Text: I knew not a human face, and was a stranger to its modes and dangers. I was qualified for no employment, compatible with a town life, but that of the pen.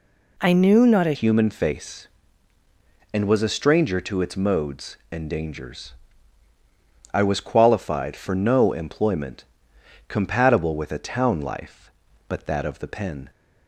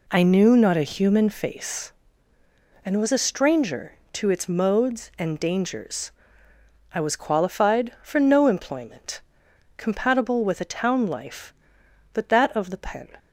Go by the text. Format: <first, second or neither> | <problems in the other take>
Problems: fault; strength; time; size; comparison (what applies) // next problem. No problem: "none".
second | changes voice at "human"; from 1.1 s on; 12.1 s long